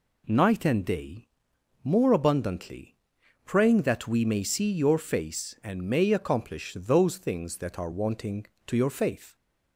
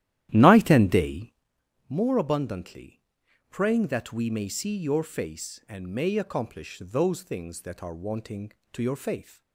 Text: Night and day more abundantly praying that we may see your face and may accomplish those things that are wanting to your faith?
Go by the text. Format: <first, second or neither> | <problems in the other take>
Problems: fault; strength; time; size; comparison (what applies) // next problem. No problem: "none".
first | starts louder than the rest; strong; until 1.5 s; 12.5 dB // pauses between "day" and "more"; noticeable; at 1.3 s; 0.56 s long; noticeable in the first // pauses between "abundantly" and "praying"; noticeable; at 3.0 s; 0.48 s long; noticeable in the first